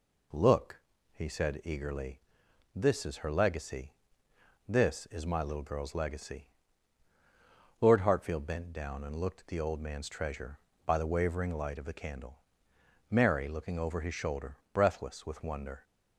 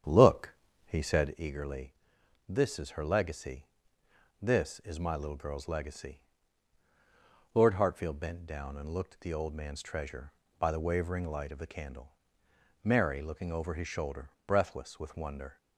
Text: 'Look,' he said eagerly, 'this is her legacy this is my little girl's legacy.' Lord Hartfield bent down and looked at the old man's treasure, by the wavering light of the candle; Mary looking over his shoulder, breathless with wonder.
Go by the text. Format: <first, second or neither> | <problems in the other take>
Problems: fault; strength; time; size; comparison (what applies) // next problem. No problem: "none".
first | starts louder than the rest; strong; until 1.4 s; 8.5 dB // pauses between "legacy" and "this"; noticeable; at 3.6 s; 0.76 s long; noticeable in the first